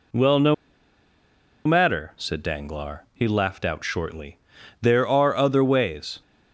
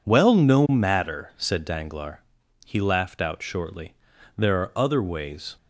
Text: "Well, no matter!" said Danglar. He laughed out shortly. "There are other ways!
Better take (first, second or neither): second